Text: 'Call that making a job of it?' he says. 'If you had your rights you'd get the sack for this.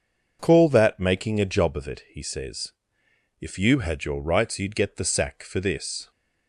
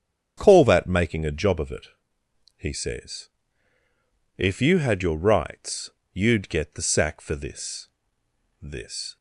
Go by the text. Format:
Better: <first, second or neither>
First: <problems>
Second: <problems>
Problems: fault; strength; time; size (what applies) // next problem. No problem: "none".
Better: first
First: none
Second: starts louder than the rest; strong; until 1.4 s; 8 dB // pauses between "rights" and "you'd"; slight; at 5.9 s; 0.22 s long // says "this" twice; at 8.6 s